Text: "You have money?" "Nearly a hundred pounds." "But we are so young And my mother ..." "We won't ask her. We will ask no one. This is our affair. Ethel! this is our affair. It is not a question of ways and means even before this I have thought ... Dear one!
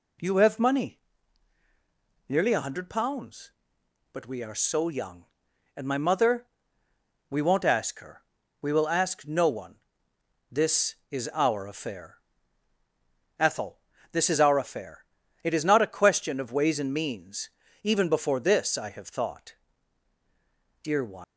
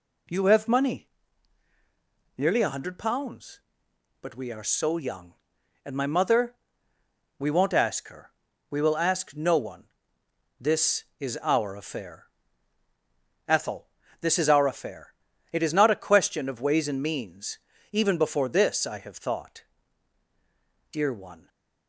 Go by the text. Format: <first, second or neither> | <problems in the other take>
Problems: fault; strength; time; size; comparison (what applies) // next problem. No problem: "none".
second | pauses between "means" and "even"; slight; at 17.4 s; 0.34 s long; slight in the second // leaves "one" unfinished; at 21.2 s; 155 ms